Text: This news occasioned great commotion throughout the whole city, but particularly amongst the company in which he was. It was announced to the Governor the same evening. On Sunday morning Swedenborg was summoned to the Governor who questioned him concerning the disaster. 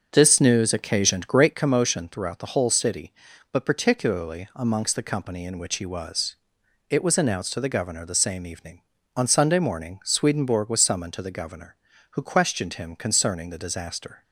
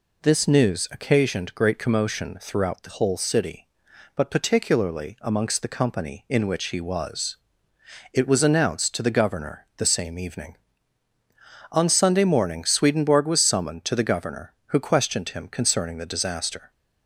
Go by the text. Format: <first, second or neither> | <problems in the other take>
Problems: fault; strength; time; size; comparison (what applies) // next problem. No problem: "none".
second | starts louder than the rest; until 1.7 s; 6.5 dB